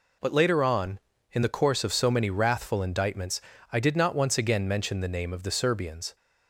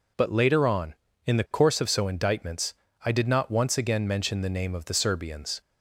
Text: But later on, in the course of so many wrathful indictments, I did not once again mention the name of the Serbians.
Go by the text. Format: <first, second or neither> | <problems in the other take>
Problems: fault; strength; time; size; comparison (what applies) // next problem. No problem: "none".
first | skips "many wrathful"; at 2.0 s